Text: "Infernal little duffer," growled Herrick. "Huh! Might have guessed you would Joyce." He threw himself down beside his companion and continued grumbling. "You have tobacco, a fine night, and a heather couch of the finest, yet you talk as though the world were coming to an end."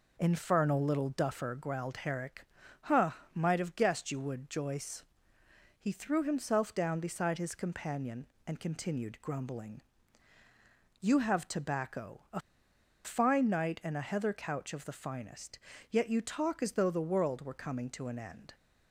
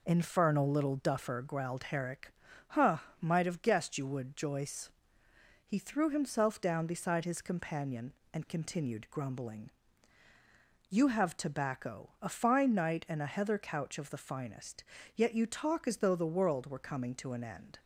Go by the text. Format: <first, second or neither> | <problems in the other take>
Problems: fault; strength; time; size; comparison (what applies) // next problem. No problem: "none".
second | pauses between "a" and "fine"; noticeable; at 12.3 s; 0.65 s long